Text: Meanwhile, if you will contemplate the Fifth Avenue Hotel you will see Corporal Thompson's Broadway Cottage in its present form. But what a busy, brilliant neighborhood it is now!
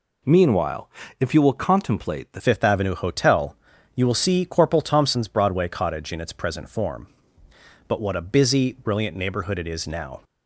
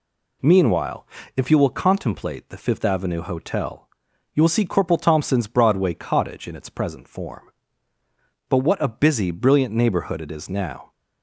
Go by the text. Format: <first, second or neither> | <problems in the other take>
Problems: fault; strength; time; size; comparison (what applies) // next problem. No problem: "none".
second | changes voice at "Fifth"; from 2.3 s on; 7.9 s long // pauses between "Hotel" and "you"; at 3.5 s; 0.40 s long; noticeable in the second